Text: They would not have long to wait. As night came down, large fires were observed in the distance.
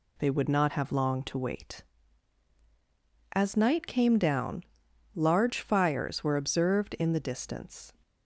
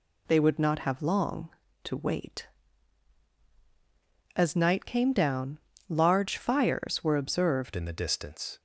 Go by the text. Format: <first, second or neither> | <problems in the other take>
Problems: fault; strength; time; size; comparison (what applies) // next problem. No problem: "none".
first | changes voice at "in"; from 7.7 s on; 0.8 s long